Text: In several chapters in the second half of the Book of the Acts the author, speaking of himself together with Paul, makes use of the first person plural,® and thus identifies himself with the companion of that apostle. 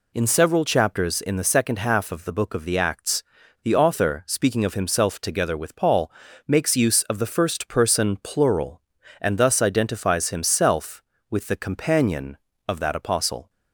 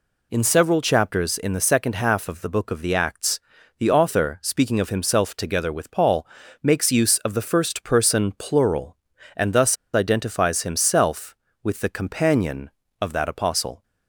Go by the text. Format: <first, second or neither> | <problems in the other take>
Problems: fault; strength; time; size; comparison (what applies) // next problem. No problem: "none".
first | pauses between "Acts" and "the"; at 3.3 s; 0.40 s long; also in the first // pauses between "thus" and "identifies"; slight; at 9.7 s; 0.18 s long